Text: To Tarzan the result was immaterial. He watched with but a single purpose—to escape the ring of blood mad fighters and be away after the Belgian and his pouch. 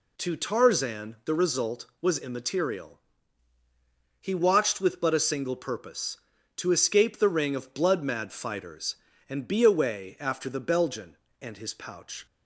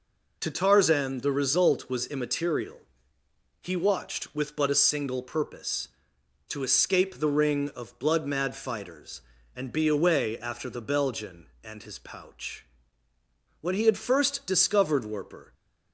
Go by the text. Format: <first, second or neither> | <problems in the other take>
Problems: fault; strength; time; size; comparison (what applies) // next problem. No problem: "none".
first | goes on to say "When he had first discovered Werper"; strong; from 13.6 s on; 1.9 s long